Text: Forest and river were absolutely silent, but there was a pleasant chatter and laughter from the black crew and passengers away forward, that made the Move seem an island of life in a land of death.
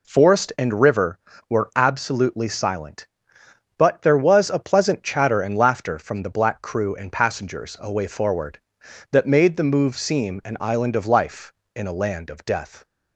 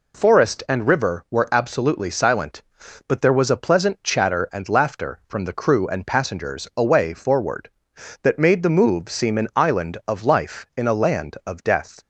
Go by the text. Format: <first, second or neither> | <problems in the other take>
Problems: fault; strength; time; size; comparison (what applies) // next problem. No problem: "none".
first | skips "black"; at 5.5 s